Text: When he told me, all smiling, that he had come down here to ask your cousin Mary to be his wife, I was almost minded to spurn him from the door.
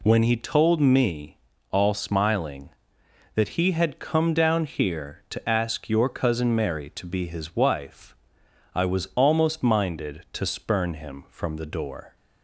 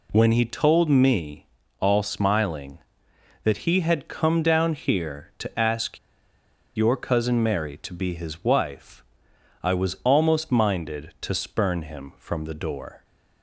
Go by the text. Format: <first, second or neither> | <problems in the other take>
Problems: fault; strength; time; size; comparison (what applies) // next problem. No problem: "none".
first | pauses between "ask" and "your"; noticeable; at 5.9 s; 0.79 s long